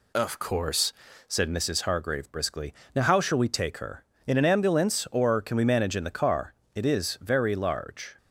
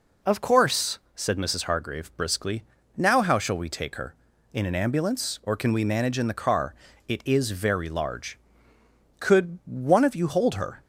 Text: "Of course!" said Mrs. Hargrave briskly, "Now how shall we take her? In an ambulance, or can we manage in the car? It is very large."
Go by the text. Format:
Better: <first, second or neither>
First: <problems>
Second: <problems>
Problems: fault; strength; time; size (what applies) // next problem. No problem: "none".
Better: first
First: none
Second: goes on to say "Could one of you hold her"; from 9.1 s on; 1.6 s long